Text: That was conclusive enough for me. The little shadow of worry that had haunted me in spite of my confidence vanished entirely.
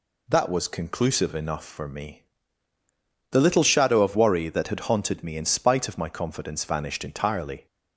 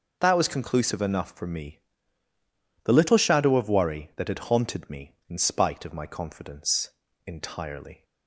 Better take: first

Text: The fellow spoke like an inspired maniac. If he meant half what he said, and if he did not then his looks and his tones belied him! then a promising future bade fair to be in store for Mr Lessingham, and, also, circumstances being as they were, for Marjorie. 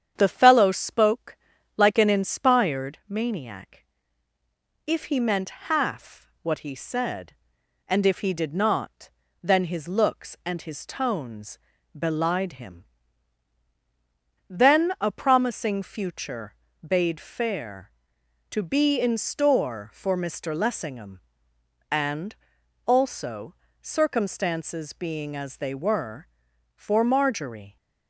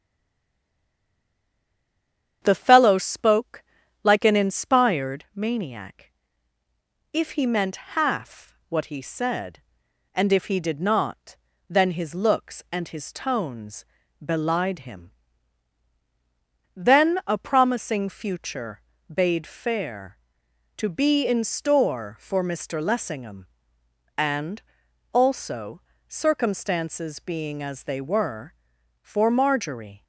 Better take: first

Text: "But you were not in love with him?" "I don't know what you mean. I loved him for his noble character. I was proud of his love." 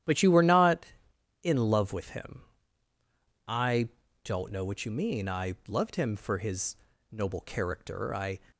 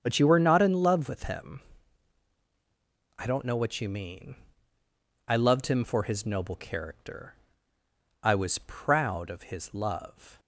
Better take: second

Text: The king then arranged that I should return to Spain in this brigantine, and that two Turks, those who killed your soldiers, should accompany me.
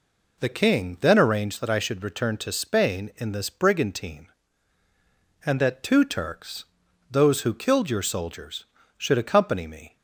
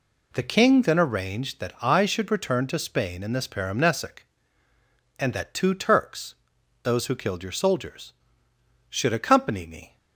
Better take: first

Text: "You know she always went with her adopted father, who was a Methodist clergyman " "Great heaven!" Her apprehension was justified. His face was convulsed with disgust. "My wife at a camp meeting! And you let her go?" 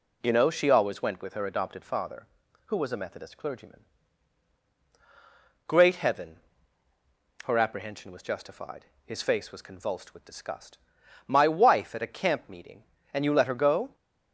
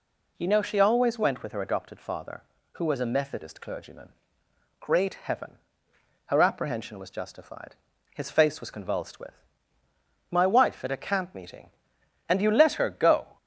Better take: first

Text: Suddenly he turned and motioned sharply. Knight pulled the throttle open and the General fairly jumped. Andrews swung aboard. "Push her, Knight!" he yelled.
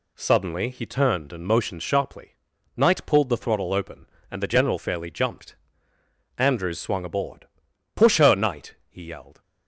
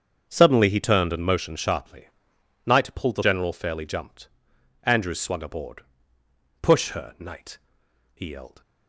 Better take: first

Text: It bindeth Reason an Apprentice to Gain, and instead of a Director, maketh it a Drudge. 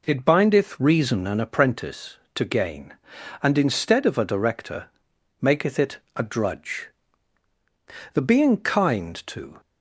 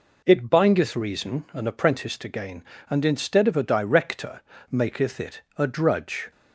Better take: second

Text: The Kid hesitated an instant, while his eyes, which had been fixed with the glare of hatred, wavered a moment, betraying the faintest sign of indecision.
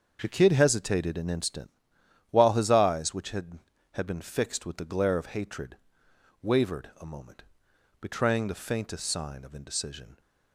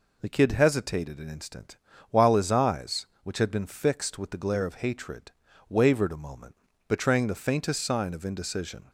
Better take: second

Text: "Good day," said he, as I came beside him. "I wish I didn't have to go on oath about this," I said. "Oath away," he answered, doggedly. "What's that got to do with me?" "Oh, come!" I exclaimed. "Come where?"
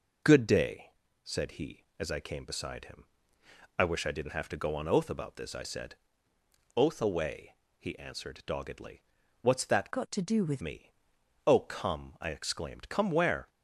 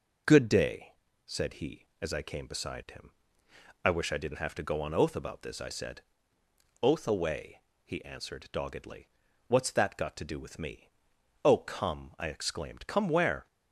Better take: second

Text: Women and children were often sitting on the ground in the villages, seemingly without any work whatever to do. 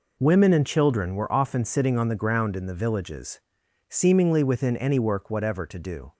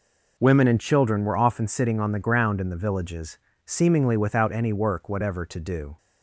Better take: second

